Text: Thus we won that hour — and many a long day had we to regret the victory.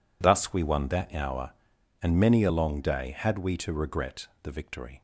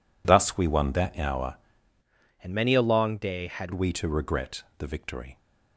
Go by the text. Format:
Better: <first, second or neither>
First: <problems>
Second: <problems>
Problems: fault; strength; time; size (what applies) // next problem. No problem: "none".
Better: first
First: pauses between "regret" and "the"; slight; at 4.2 s; 0.16 s long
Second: changes voice from "and" to "had"; from 2.4 to 3.7 s; 1.3 s long // pauses between "regret" and "the"; slight; at 4.6 s; 0.16 s long